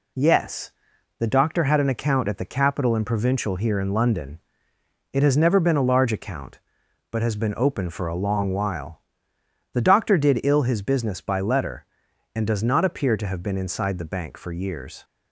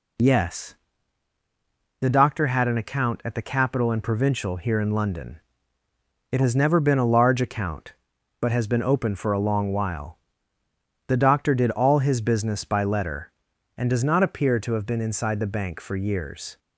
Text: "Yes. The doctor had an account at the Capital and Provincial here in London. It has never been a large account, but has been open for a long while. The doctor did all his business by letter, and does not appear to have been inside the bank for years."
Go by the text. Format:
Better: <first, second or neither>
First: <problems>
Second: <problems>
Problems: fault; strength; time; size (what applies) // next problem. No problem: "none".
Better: second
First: says "ill" for "all"; at 10.4 s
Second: none